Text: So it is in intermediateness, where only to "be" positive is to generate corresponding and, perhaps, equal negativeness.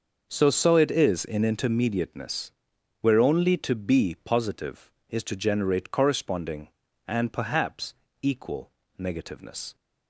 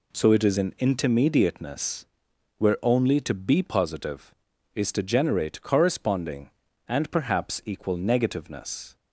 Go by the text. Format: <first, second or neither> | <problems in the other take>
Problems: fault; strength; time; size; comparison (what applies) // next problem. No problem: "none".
second | starts louder than the rest; noticeable; until 1.3 s; 6 dB // says "So" twice; at 0.4 s // pauses between "equal" and "negativeness"; slight; at 8.6 s; 0.30 s long